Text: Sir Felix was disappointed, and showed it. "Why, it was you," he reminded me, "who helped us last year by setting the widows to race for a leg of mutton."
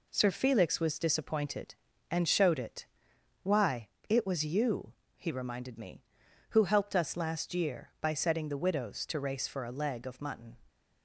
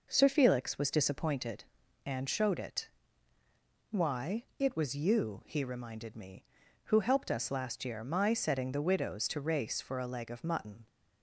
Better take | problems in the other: first | says "my" for "by"; at 8.0 s

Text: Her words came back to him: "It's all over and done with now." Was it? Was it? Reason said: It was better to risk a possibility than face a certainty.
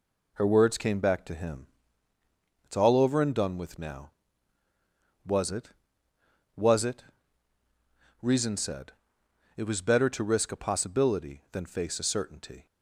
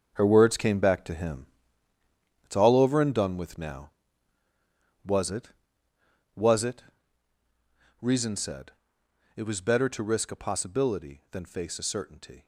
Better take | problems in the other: first | gets quieter; strong; throughout; 10 dB

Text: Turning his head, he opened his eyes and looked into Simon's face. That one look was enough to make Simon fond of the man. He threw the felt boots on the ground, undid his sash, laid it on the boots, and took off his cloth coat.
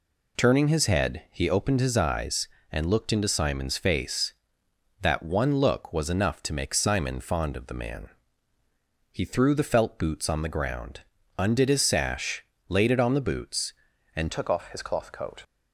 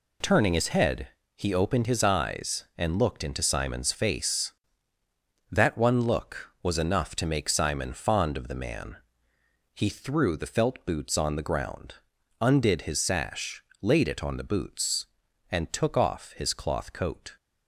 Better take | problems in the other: second | changes voice at "took"; from 14.2 s on; 1.2 s long

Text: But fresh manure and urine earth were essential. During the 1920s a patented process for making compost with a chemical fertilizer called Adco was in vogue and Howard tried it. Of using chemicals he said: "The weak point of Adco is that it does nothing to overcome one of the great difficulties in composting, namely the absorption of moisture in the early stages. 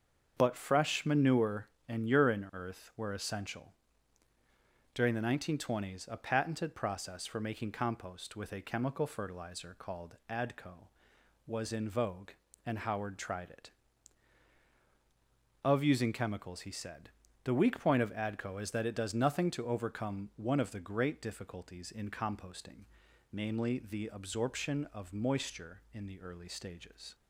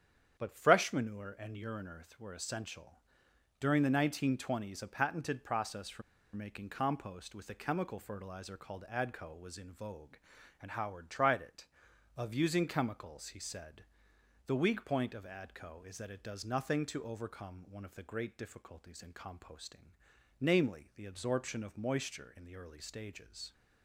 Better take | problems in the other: first | starts louder than the rest; strong; until 1.4 s; 8.5 dB; also in the first // pauses between "for" and "making"; slight; at 6.0 s; 0.32 s long

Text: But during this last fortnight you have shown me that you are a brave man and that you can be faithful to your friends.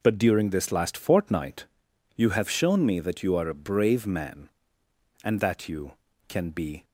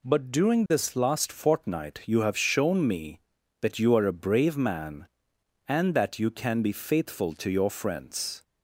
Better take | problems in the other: second | pauses between "fortnight" and "you"; noticeable; at 1.6 s; 0.50 s long // stops before "faithful to your friends"; at 6.8 s

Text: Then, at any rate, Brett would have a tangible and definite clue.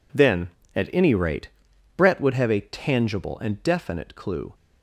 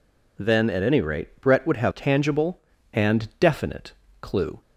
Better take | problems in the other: first | skips "a"; at 1.9 s // pauses between "definite" and "clue"; slight; at 3.9 s; 0.30 s long

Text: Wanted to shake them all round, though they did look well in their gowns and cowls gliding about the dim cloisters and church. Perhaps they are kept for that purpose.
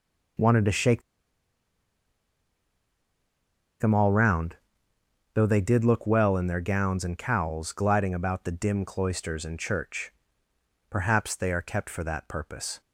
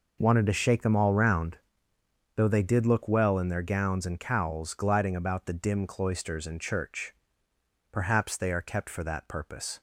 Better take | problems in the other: second | pauses between "shake" and "them"; strong; at 1.0 s; 2.7 s long

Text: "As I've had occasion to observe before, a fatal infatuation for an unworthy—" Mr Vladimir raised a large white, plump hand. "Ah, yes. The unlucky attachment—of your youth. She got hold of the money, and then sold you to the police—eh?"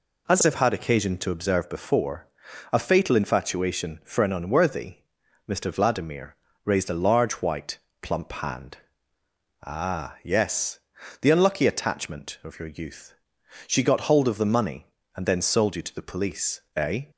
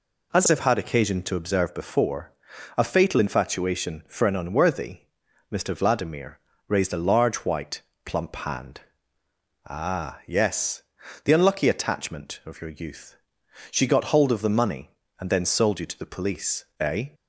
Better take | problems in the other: neither | pauses between "Vladimir" and "raised"; slight; the same in both

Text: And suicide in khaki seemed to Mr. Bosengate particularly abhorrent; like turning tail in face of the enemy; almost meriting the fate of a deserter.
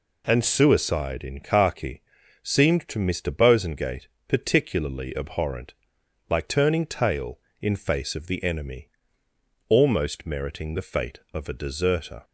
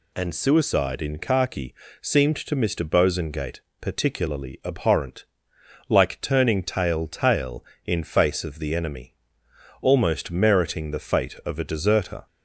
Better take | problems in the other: first | pauses between "khaki" and "seemed"; slight; at 1.7 s; 0.30 s long; also in the first // pauses between "Bosengate" and "particularly"; slight; at 3.6 s; 0.20 s long; slight in the first // says "tail" twice; at 7.0 s

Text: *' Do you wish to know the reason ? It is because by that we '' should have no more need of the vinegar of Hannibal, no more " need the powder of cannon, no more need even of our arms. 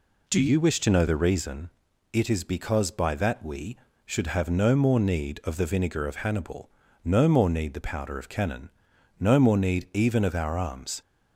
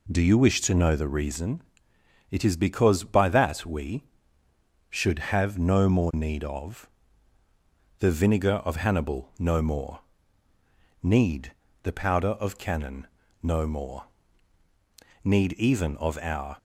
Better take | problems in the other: first | pauses between "of" and "the"; at 6.8 s; 1.1 s long // pauses between "need" and "the"; slight; at 11.5 s; 0.30 s long // pauses between "more" and "need"; at 14.0 s; 1.1 s long // stops before "arms"; at 16.5 s

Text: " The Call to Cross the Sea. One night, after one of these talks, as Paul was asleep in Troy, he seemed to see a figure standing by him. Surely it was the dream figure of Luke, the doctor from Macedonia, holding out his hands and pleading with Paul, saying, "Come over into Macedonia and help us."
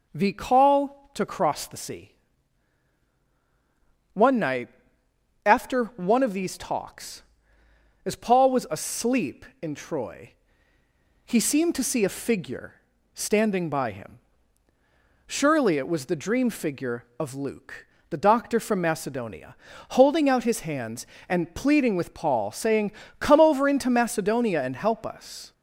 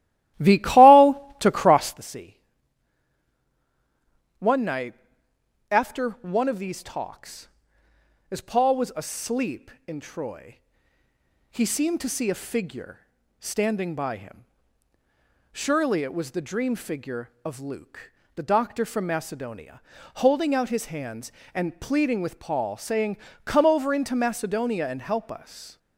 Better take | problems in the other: first | starts louder than the rest; strong; until 2.0 s; 15 dB // pauses between "figure" and "standing"; at 12.9 s; 0.38 s long; also in the first

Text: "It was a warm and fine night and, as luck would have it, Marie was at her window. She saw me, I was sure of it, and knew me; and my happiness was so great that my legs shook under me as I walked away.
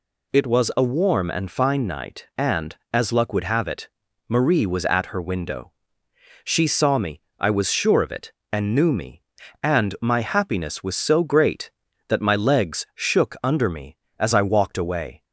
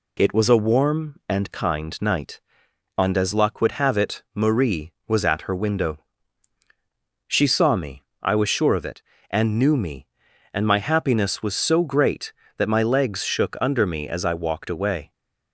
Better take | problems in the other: first | says "kind" for "fine"; at 1.5 s

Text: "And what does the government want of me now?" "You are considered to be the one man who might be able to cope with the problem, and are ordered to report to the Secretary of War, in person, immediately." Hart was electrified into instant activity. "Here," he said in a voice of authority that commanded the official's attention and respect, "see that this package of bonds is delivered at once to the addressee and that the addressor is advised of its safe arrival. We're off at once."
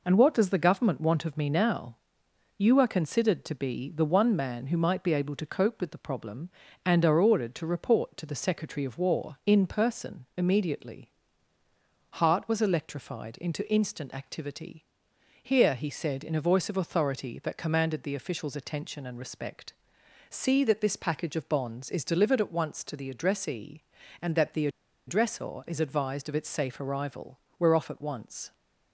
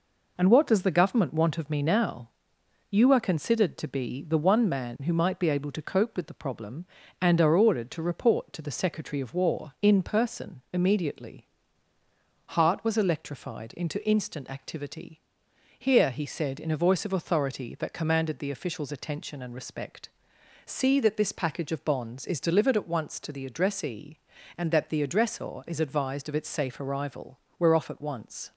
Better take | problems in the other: second | pauses between "the" and "addressor"; at 24.6 s; 0.38 s long

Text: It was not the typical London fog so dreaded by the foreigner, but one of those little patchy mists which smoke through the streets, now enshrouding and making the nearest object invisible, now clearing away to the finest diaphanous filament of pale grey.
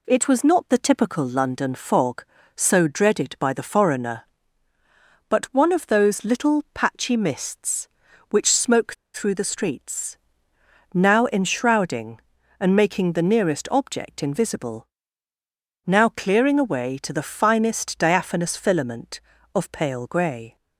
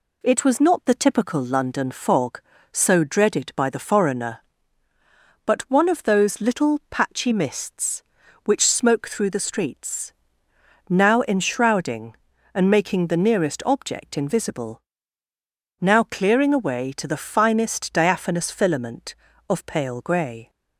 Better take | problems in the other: second | pauses between "smoke" and "through"; slight; at 8.9 s; 0.20 s long

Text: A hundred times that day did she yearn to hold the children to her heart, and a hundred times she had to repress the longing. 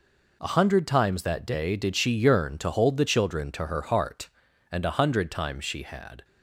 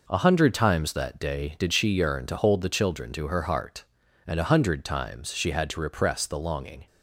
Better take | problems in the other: second | stops before "to repress the longing"; at 6.2 s

